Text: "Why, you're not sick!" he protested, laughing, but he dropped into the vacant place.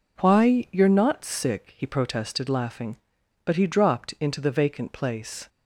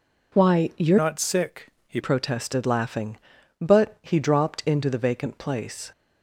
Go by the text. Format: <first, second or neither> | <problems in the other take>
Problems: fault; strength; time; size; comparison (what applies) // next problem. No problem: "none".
first | changes voice from "not" to "he"; from 0.9 to 1.9 s; 1.0 s long